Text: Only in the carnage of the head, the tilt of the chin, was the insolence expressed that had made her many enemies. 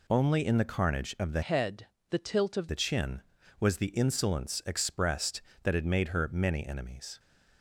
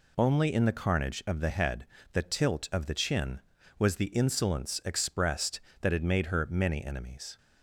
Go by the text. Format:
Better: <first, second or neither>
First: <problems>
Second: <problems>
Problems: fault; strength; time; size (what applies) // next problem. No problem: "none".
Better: second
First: changes voice from "head" to "of"; from 1.4 to 2.6 s; 1.2 s long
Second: none